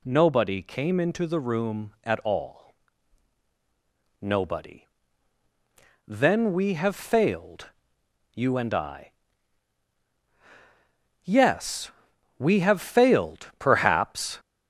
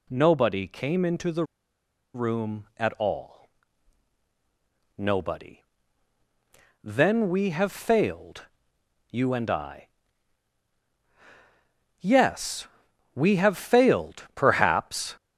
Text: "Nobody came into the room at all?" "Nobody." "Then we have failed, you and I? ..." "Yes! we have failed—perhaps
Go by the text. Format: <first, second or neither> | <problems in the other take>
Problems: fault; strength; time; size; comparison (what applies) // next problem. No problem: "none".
first | pauses between "the" and "room"; noticeable; at 1.4 s; 0.70 s long